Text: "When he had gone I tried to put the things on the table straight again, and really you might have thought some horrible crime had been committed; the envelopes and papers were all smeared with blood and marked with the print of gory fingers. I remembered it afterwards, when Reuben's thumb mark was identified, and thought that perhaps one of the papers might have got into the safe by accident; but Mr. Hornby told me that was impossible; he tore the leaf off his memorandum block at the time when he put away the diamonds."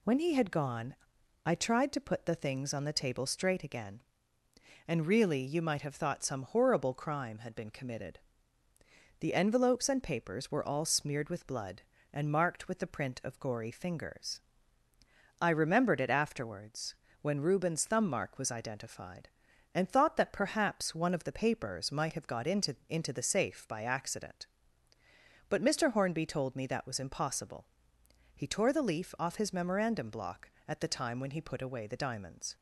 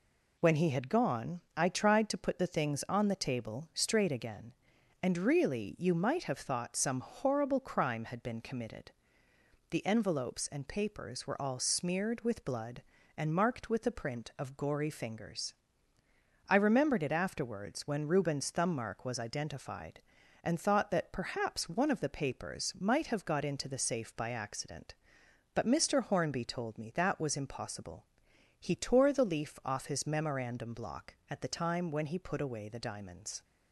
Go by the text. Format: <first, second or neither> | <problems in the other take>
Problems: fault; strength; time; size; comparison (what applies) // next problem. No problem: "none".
second | pauses between "gone" and "I"; noticeable; at 0.9 s; 0.50 s long // says "into" twice; at 22.8 s